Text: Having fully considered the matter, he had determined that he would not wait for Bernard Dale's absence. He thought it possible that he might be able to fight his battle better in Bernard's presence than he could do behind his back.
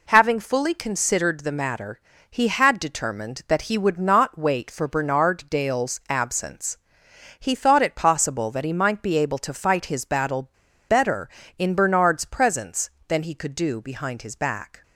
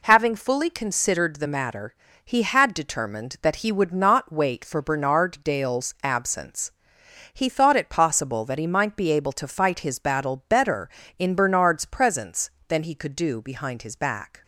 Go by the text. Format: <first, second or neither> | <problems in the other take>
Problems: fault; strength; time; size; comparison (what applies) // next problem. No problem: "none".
second | pauses between "battle" and "better"; at 10.4 s; 0.39 s long